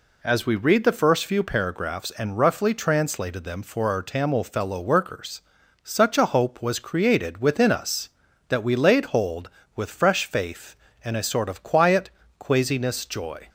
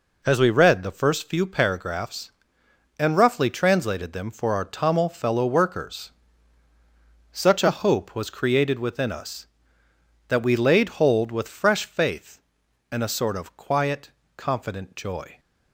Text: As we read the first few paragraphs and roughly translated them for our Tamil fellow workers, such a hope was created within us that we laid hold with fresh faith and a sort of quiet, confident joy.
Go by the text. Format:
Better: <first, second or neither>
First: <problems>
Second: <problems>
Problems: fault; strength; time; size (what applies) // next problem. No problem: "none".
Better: second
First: says "quasiness" for "confident"; at 12.3 s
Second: none